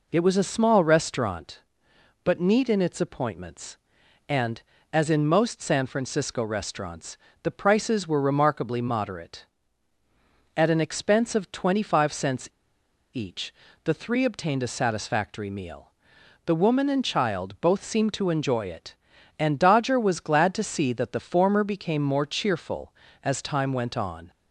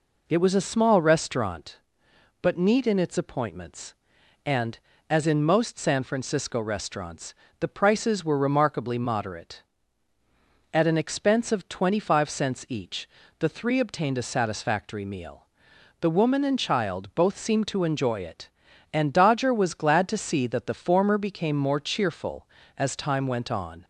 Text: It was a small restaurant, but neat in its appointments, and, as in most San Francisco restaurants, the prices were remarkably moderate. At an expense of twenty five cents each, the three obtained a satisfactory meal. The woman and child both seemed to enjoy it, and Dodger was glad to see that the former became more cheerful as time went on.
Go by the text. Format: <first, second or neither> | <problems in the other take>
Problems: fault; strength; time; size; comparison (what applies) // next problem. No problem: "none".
second | pauses between "cents" and "each"; noticeable; at 12.4 s; 0.65 s long